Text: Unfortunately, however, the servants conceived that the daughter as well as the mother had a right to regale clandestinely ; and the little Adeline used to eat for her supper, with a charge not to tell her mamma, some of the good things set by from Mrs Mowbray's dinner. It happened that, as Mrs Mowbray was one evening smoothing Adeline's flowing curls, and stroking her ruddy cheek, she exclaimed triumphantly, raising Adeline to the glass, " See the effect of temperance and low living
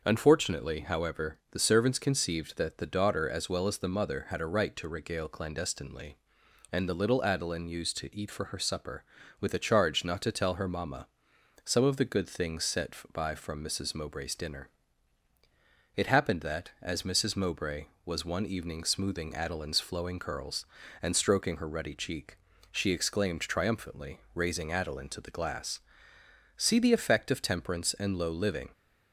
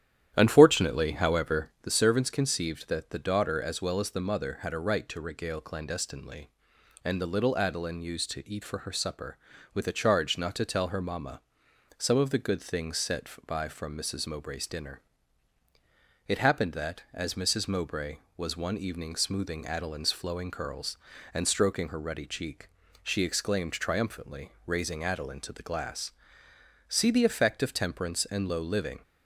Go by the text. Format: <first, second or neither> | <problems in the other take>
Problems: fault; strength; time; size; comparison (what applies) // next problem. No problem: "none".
first | starts louder than the rest; strong; until 1.9 s; 11 dB